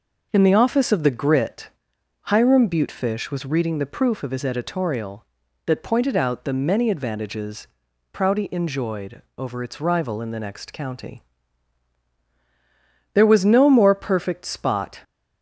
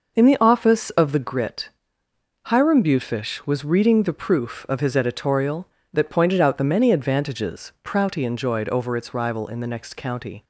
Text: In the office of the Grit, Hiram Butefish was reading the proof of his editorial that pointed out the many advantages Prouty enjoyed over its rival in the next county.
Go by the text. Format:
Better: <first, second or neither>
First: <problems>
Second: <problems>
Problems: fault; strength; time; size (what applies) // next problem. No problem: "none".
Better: second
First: pauses between "advantages" and "Prouty"; noticeable; at 7.6 s; 0.46 s long // pauses between "enjoyed" and "over"; slight; at 9.2 s; 0.16 s long // goes on to say "There was no more perfect spot"; strong; from 13.1 s on; 1.8 s long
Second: none